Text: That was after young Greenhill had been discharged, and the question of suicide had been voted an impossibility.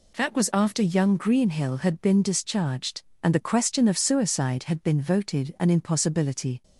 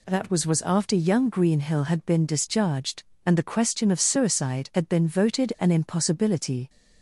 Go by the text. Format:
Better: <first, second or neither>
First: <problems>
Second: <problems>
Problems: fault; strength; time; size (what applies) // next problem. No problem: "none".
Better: first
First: none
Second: says "was" twice; at 0.4 s